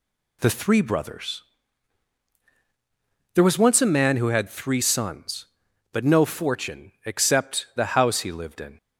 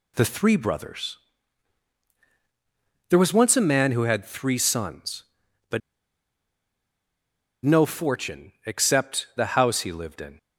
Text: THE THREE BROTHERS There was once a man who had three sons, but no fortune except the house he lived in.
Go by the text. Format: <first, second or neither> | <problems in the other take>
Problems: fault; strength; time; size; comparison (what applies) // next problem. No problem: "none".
first | pauses between "BROTHERS" and "There"; strong; at 1.1 s; 1.9 s long; strong in the first // pauses between "but" and "no"; strong; at 5.8 s; 1.8 s long // pauses between "fortune" and "except"; slight; at 8.5 s; 0.16 s long; slight in the first